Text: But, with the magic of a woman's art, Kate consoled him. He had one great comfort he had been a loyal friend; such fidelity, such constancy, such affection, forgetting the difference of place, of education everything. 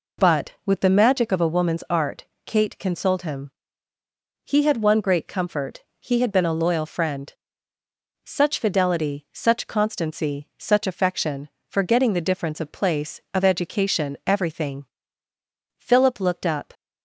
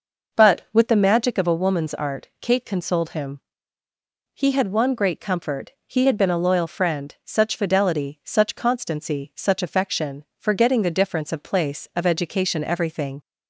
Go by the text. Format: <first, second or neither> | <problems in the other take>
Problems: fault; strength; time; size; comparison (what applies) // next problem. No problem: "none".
second | pauses between "comfort" and "he"; slight; at 5.8 s; 0.20 s long // goes on to say "Philip looked up"; noticeable; from 15.7 s on; 0.96 s long